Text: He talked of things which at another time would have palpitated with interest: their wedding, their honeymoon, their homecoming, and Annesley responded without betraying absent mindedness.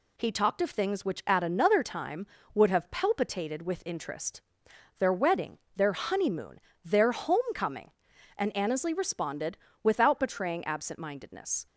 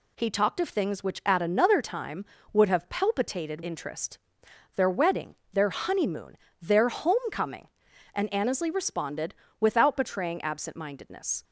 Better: first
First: pauses between "responded" and "without"; slight; at 9.5 s; 0.24 s long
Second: skips "with"; at 3.6 s // pauses between "responded" and "without"; slight; at 9.3 s; 0.24 s long

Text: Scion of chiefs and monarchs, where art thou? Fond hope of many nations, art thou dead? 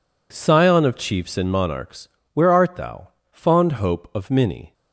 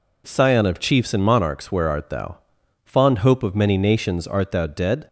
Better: second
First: stops before "nations art thou dead"; at 4.7 s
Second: none

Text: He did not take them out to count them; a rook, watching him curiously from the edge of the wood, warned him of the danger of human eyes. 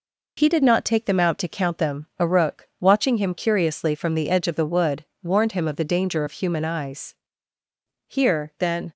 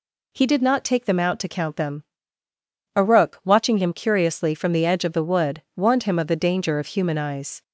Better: second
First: goes on to say "Here then"; noticeable; from 8.0 s on; 0.88 s long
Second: none

